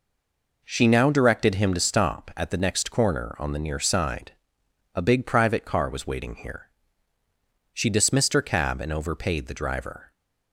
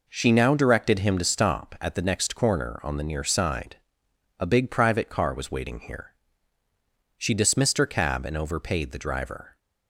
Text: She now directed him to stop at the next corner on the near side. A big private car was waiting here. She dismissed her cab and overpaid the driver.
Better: second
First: stays silent before the first word; slight; until 0.6 s; 0.6 s long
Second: none

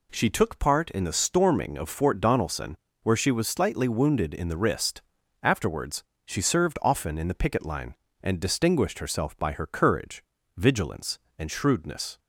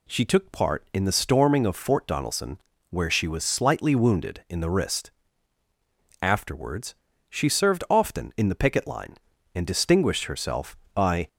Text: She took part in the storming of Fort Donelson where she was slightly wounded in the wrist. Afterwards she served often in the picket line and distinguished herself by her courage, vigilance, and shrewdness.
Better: first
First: pauses between "Donelson" and "where"; slight; at 2.7 s; 0.28 s long // pauses between "Afterwards" and "she"; slight; at 6.0 s; 0.22 s long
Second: pauses between "Donelson" and "where"; slight; at 2.5 s; 0.32 s long // pauses between "Afterwards" and "she"; slight; at 6.9 s; 0.34 s long // stops before "her courage vigilance and shrewdness"; at 11.2 s

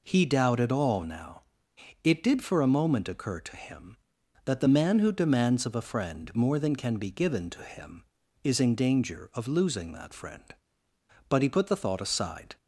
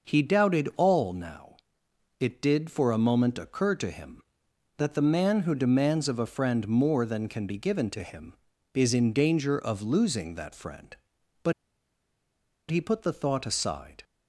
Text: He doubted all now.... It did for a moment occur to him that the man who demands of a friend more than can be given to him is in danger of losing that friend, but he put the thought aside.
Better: first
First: none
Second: pauses between "but" and "he"; at 11.5 s; 1.1 s long

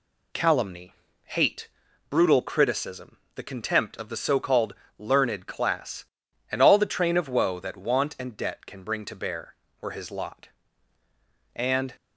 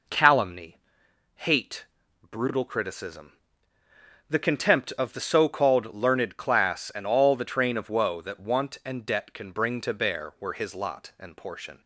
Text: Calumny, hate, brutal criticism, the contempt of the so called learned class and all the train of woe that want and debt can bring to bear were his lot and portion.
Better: second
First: pauses between "called" and "learned"; slight; at 4.7 s; 0.24 s long // stops before "portion"; at 11.9 s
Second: none

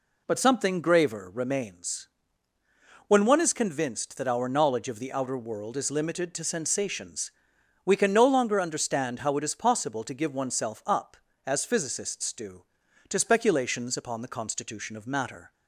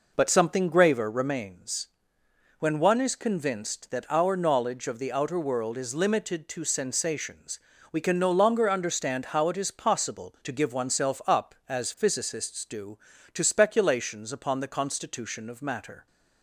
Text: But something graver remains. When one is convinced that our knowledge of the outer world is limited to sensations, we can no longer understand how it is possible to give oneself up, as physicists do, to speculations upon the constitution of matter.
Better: neither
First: none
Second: none

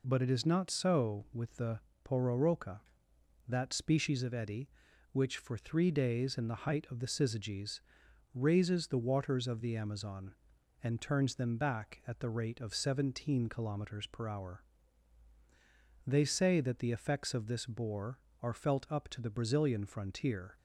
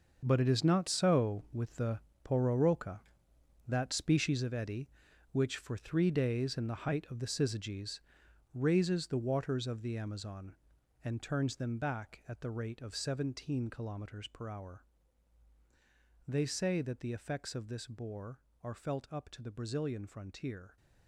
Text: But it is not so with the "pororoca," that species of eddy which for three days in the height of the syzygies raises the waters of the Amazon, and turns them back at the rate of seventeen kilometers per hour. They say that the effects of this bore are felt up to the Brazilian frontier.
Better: first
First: pauses between "the" and "pororoca"; slight; at 1.7 s; 0.24 s long // pauses between "syzygies" and "raises"; noticeable; at 7.7 s; 0.54 s long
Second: gets quieter; strong; throughout; 12.5 dB // pauses between "the" and "pororoca"; slight; at 1.9 s; 0.24 s long // pauses between "syzygies" and "raises"; noticeable; at 7.9 s; 0.54 s long

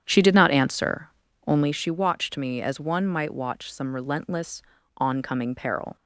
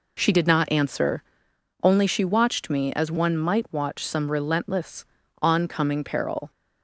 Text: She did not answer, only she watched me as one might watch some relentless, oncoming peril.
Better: second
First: starts louder than the rest; strong; until 1.9 s; 9 dB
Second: none

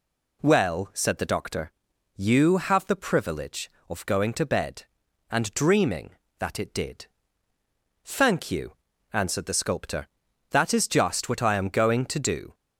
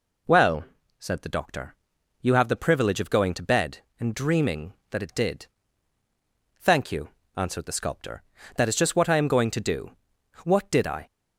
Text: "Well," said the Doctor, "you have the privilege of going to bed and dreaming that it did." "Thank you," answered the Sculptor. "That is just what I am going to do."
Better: first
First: none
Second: goes on to say "What did I"; noticeable; from 10.4 s on; 0.62 s long

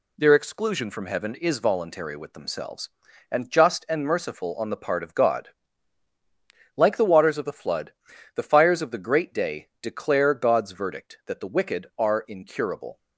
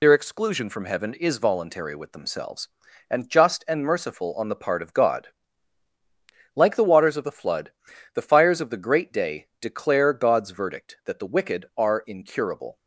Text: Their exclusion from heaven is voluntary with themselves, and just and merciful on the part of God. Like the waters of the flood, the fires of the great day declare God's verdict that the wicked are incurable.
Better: first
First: none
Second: loses the start of "Their"; at 0.0 s; 55 ms

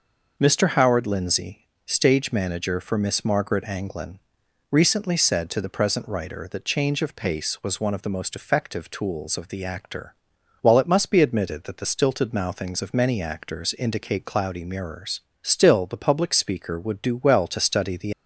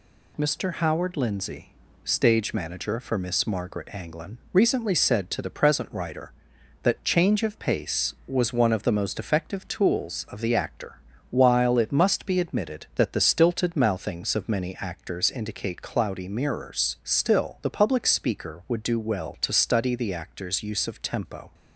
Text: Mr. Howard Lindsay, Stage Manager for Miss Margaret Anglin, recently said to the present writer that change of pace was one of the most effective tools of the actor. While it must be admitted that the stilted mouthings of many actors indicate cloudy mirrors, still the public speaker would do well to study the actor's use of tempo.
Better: second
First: stops before "actor's use of tempo"; at 18.1 s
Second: none

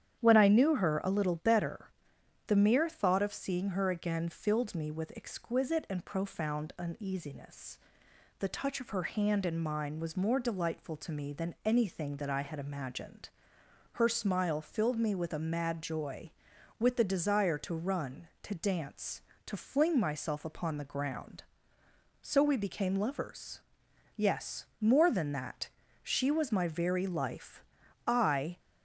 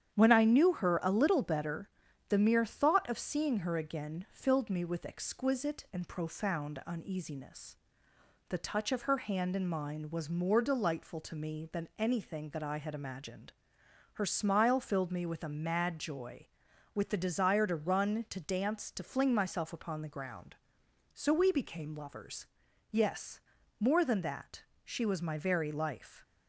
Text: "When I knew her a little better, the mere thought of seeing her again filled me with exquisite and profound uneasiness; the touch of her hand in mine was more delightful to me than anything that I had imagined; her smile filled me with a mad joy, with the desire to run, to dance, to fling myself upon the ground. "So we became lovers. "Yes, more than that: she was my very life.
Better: second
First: starts louder than the rest; strong; until 1.2 s; 9.5 dB // goes on to say "I"; from 28.0 s on; 0.54 s long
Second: starts louder than the rest; strong; until 1.1 s; 9.5 dB

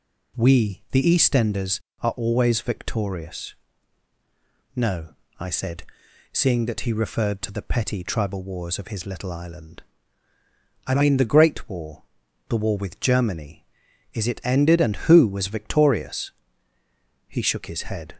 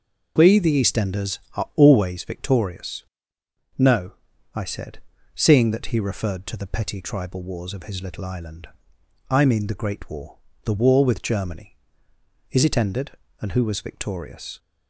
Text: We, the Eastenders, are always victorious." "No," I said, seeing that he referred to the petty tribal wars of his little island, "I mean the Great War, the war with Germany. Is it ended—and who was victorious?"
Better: second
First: goes on to say "He shook his head"; noticeable; from 17.2 s on; 0.86 s long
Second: none

